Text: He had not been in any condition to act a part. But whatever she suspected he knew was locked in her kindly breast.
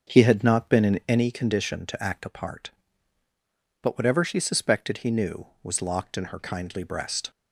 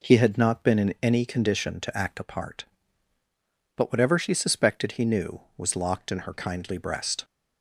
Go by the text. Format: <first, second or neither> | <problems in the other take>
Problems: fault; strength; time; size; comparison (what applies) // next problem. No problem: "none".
second | starts louder than the rest; until 1.3 s; 6.5 dB